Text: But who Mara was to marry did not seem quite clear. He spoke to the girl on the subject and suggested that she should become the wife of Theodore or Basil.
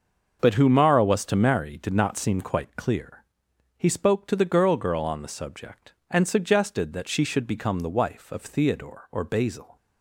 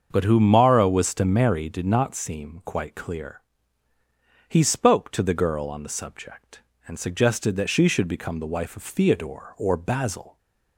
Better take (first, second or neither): second